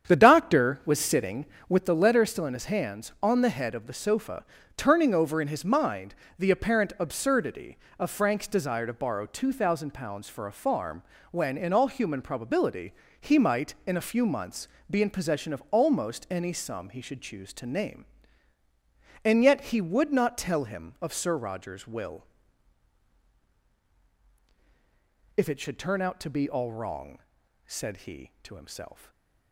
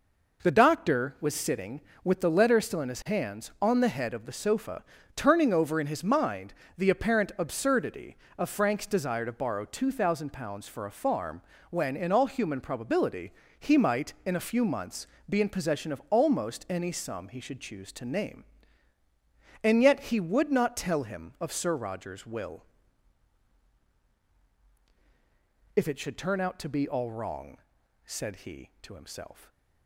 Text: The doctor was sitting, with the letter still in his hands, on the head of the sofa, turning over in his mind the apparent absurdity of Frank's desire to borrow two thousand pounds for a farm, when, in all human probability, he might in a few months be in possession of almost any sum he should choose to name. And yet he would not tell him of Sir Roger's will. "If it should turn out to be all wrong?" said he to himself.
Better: second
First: starts louder than the rest; strong; until 1.9 s; 8.5 dB // pauses between "mind" and "the"; slight; at 6.1 s; 0.24 s long // pauses between "months" and "be"; slight; at 14.6 s; 0.24 s long // stays silent after the last word; slight; from 28.9 s on; 0.6 s long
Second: pauses between "mind" and "the"; slight; at 6.5 s; 0.24 s long // pauses between "months" and "be"; slight; at 15.0 s; 0.24 s long

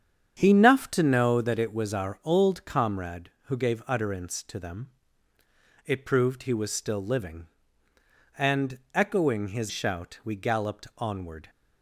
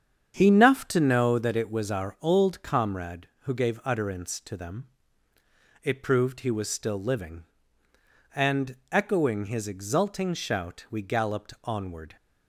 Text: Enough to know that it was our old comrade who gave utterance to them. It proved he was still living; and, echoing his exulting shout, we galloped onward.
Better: second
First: starts louder than the rest; strong; until 1.4 s; 8 dB // skips "exulting"; at 9.6 s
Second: starts louder than the rest; strong; until 1.3 s; 8 dB

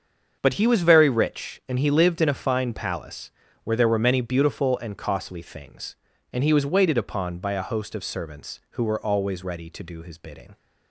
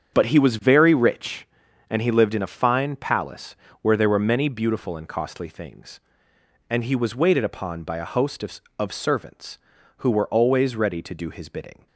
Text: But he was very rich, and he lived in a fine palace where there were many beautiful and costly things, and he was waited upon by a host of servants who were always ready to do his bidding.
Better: first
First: starts louder than the rest; until 1.4 s; 7 dB // pauses between "palace" and "where"; slight; at 3.3 s; 0.34 s long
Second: starts louder than the rest; strong; until 1.2 s; 7.5 dB // pauses between "palace" and "where"; slight; at 3.5 s; 0.28 s long // says "of" twice; at 8.7 s

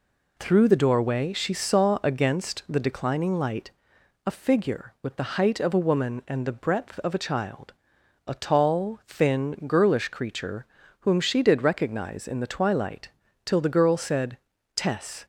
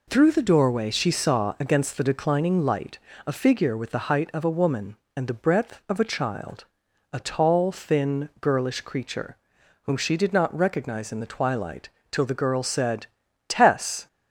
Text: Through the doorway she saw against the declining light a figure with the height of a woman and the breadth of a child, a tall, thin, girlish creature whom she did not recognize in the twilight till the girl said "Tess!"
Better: second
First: pauses between "light" and "a"; noticeable; at 3.7 s; 0.54 s long // pauses between "creature" and "whom"; slight; at 10.6 s; 0.36 s long // skips "not"; at 11.6 s // pauses between "twilight" and "till"; slight; at 13.0 s; 0.36 s long // pauses between "said" and "Tess"; at 14.3 s; 0.38 s long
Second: pauses between "light" and "a"; slight; at 2.9 s; 0.30 s long // pauses between "creature" and "whom"; noticeable; at 9.3 s; 0.46 s long // pauses between "twilight" and "till"; slight; at 11.8 s; 0.20 s long // pauses between "said" and "Tess"; at 13.0 s; 0.42 s long

